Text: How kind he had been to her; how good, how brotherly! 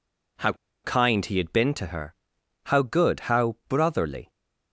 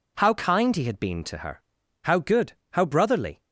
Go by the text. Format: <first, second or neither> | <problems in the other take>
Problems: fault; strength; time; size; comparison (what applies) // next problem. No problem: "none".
second | pauses between "How" and "kind"; slight; at 0.5 s; 0.32 s long